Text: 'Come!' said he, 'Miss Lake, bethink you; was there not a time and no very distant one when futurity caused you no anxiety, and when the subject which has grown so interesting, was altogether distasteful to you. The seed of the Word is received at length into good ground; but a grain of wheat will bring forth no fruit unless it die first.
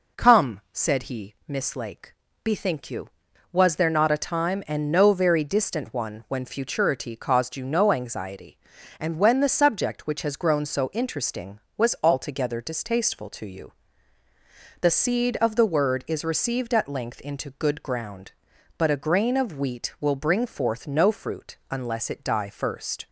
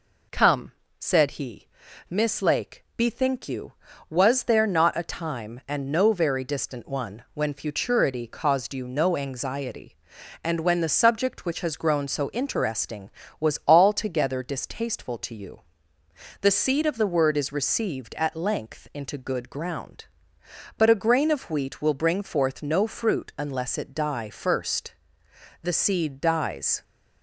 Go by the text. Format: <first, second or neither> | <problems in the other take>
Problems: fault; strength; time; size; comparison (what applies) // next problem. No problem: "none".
first | goes on to say "The seed dies"; noticeable; from 25.6 s on; 1.2 s long